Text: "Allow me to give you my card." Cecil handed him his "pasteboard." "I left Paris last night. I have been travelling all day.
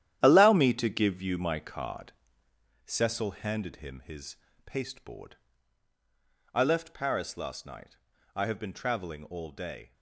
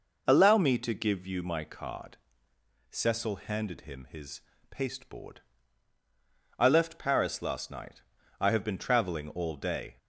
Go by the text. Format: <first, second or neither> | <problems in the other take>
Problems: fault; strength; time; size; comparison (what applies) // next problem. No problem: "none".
second | gets quieter; strong; throughout; 10.5 dB // pauses between "his" and "pasteboard"; slight; at 4.3 s; 0.30 s long; slight in the second